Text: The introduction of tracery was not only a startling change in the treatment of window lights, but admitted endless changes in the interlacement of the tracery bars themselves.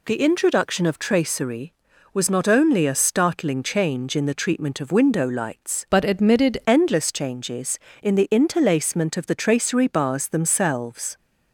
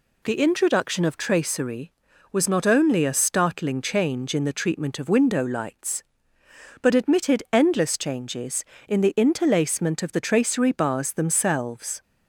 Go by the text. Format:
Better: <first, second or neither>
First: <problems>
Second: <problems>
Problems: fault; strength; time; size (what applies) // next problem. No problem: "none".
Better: second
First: changes voice from "but" to "admitted"; from 5.9 to 6.6 s; 0.7 s long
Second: none